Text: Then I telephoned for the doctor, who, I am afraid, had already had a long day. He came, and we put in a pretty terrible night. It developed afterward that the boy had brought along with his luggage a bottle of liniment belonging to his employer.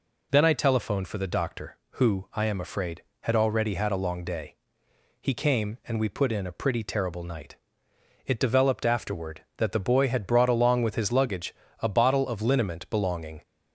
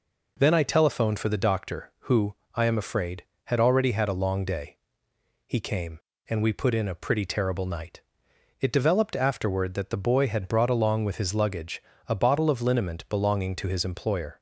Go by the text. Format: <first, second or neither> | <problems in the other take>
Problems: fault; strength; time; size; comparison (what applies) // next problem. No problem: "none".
second | pauses between "luggage" and "a"; slight; at 11.5 s; 0.26 s long; slight in the second // stops before "to his employer"; at 13.4 s